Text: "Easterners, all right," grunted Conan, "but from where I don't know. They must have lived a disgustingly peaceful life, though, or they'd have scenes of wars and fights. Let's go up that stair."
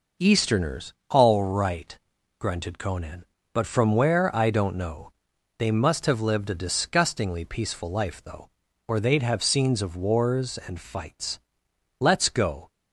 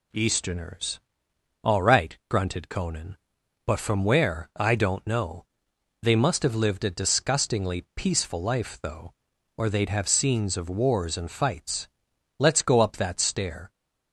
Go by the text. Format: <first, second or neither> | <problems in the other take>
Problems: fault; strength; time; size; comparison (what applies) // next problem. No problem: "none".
second | stops before "up that stair"; at 12.7 s